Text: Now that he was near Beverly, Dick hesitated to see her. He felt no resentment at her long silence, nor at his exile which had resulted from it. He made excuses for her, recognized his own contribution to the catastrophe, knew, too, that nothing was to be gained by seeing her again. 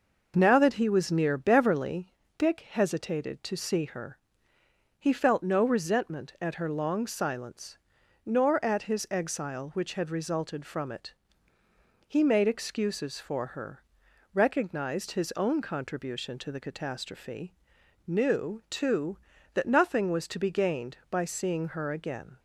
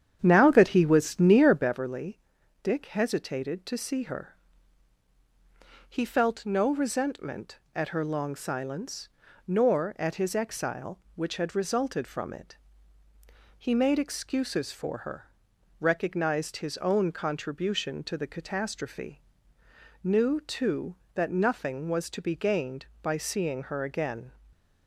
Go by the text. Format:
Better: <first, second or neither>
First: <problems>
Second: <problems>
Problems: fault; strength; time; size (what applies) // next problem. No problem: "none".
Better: first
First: none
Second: starts louder than the rest; strong; until 1.8 s; 9 dB // stays silent after the last word; slight; from 24.3 s on; 0.5 s long